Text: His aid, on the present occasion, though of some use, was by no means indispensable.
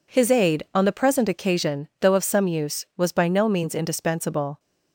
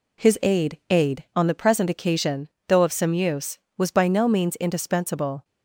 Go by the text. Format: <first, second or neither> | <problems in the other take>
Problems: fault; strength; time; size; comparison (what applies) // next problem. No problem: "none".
first | says "aid" twice; at 0.9 s